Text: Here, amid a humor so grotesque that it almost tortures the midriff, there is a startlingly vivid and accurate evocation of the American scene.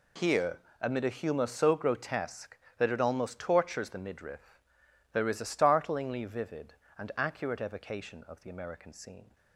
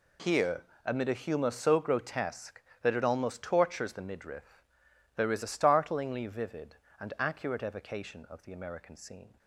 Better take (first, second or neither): neither